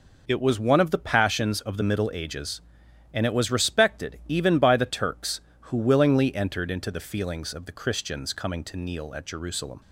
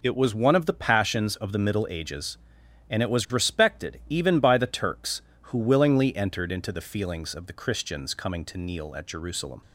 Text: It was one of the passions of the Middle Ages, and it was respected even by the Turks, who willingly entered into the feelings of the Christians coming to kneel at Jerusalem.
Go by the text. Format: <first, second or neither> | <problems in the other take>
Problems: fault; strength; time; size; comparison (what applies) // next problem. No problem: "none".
neither | none